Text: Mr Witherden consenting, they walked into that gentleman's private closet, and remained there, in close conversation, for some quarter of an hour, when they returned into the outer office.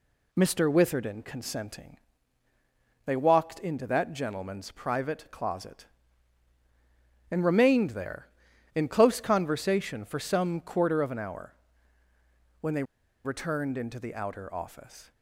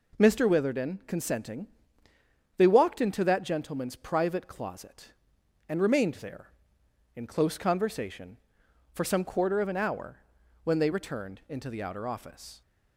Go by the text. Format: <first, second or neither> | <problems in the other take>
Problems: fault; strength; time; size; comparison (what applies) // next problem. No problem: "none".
second | pauses between "they" and "returned"; at 12.8 s; 0.41 s long